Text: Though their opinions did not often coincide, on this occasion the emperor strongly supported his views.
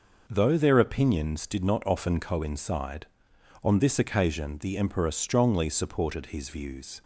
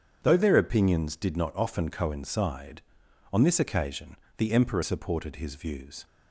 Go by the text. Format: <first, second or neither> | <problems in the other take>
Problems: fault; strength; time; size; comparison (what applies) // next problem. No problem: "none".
first | starts louder than the rest; strong; until 1.2 s; 7.5 dB // pauses between "occasion" and "the"; slight; at 4.1 s; 0.22 s long // skips "strongly"; at 4.8 s